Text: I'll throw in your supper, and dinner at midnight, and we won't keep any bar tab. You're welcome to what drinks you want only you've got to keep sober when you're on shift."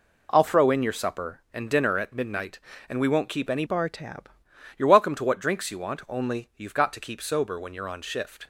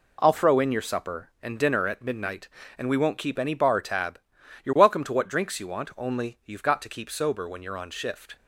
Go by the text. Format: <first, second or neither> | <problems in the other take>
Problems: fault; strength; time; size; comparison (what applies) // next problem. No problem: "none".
second | changes voice from "bar" to "tab"; from 3.6 to 4.2 s; 0.6 s long